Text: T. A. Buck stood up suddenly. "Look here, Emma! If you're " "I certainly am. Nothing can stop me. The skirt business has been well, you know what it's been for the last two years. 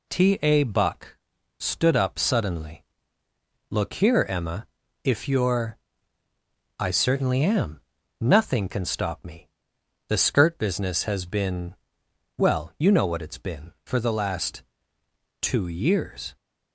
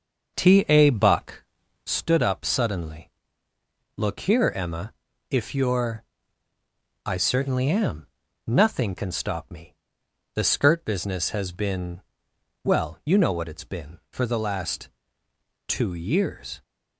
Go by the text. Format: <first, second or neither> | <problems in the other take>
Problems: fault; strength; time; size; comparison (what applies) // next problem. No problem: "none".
first | starts louder than the rest; until 2.1 s; 6.5 dB // pauses between "Buck" and "stood"; at 1.4 s; 0.44 s long; also in the first // pauses between "been" and "well"; noticeable; at 12.0 s; 0.62 s long; noticeable in the first // pauses between "last" and "two"; noticeable; at 14.8 s; 0.80 s long; noticeable in the first